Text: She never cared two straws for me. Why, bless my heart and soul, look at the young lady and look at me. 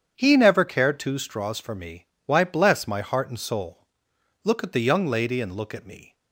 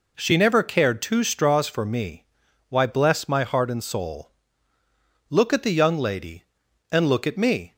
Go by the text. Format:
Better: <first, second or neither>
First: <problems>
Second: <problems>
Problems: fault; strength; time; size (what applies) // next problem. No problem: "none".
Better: second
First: starts louder than the rest; strong; until 1.2 s; 8 dB // says "He" for "She"; at 0.1 s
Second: none